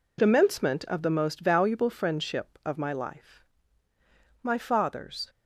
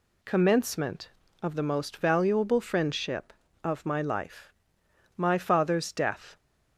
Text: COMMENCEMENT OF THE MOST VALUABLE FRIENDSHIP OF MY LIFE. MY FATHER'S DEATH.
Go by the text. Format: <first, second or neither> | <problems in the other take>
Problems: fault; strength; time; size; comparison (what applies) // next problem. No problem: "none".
second | stops before "DEATH"; at 5.2 s